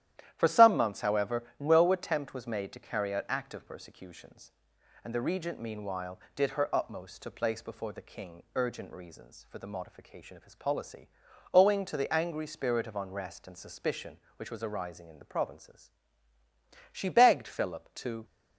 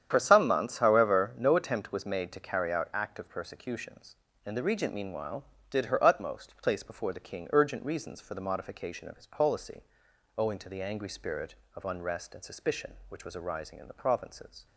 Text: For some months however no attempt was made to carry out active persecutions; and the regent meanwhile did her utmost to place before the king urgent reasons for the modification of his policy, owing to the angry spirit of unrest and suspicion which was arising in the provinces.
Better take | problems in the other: second | starts louder than the rest; strong; until 1.3 s; 12 dB; strong in the second // pauses between "however" and "no"; slight; at 1.4 s; 0.16 s long // goes on to say "She begged Philip to"; from 16.9 s on; 1.3 s long

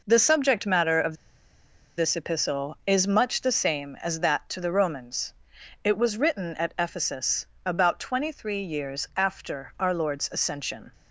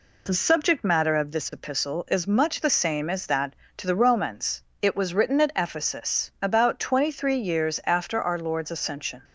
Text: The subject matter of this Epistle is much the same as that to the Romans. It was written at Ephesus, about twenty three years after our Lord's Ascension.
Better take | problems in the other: second | pauses between "of" and "this"; noticeable; at 1.1 s; 0.83 s long

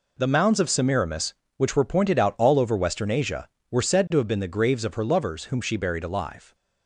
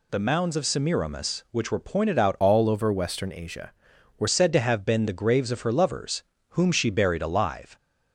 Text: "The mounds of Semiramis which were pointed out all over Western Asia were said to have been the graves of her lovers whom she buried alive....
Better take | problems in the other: first | changes voice from "all" to "were"; from 2.3 to 4.2 s; 1.9 s long // pauses between "lovers" and "whom"; slight; at 6.2 s; 0.28 s long

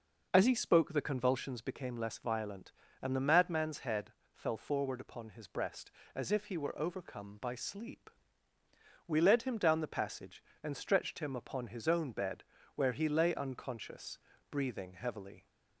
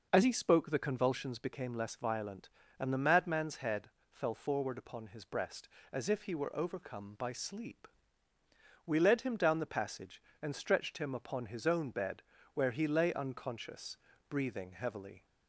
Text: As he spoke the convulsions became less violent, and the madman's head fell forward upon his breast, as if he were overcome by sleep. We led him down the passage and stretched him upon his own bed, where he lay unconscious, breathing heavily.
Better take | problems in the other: neither | pauses between "head" and "fell"; slight; the same in both

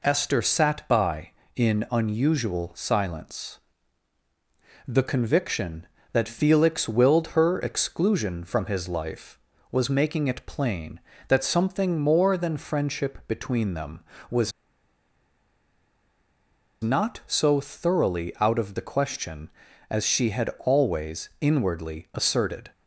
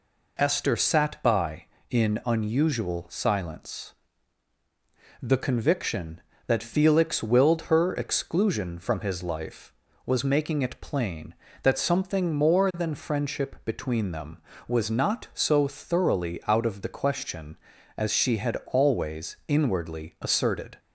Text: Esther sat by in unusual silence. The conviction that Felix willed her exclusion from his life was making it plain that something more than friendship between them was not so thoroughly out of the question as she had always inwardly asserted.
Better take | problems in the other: second | pauses between "was" and "not"; strong; at 14.5 s; 2.3 s long

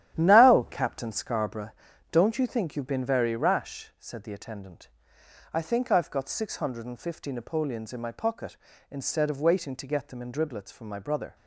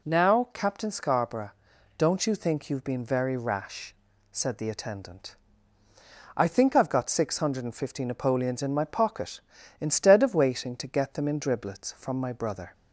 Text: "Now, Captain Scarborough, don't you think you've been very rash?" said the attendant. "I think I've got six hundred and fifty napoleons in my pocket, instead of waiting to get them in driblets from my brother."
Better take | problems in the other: second | gets quieter; strong; throughout; 9 dB

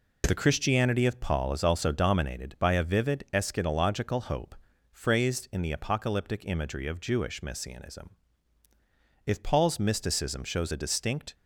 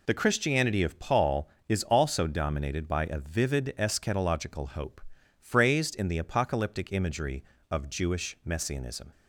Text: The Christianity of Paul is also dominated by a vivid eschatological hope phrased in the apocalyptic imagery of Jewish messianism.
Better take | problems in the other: second | pauses between "hope" and "phrased"; slight; at 4.5 s; 0.36 s long; slight in the second // goes on to say "If Paul's mysticism shows a distinct"; strong; from 9.2 s on; 2.0 s long

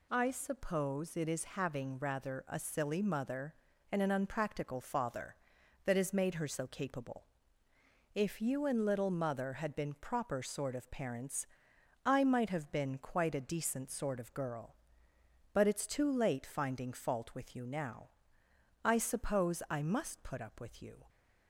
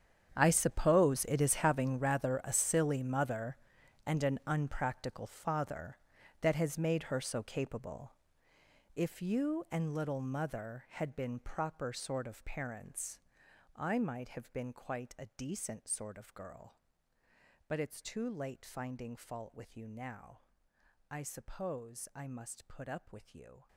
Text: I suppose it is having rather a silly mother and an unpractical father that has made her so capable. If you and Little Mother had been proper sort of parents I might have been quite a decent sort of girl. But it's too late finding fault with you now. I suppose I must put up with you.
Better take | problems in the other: first | gets quieter; strong; throughout; 17.5 dB // pauses between "parents" and "I"; noticeable; at 13.1 s; 0.58 s long; noticeable in the first

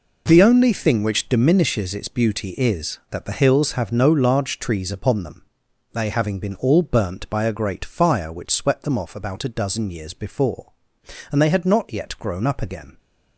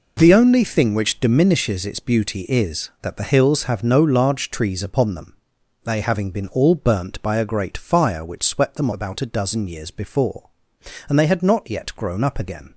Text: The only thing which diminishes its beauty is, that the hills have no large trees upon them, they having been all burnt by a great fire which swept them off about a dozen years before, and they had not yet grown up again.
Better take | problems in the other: first | skips "off"; at 8.9 s

